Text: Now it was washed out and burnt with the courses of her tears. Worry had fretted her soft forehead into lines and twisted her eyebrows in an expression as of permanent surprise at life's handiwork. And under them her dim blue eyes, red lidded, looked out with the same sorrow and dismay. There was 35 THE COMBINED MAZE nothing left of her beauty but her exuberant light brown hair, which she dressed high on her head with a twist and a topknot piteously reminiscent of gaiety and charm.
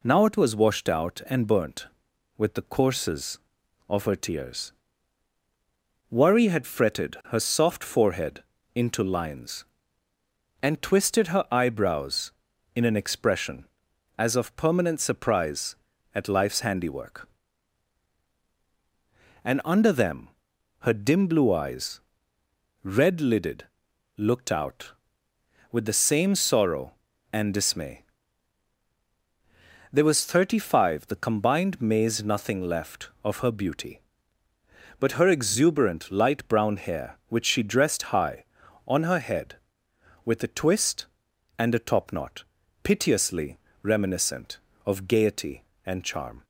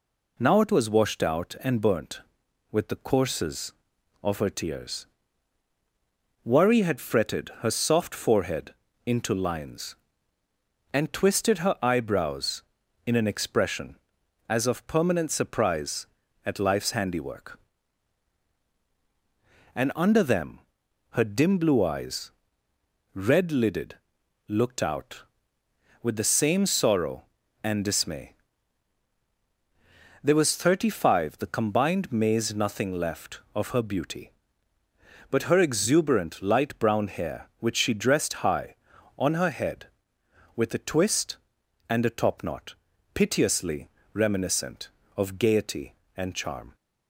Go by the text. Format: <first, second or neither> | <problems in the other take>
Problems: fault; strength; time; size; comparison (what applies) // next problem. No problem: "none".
neither | pauses between "forehead" and "into"; slight; the same in both // pauses between "them" and "her"; noticeable; the same in both // pauses between "topknot" and "piteously"; the same in both // pauses between "piteously" and "reminiscent"; slight; the same in both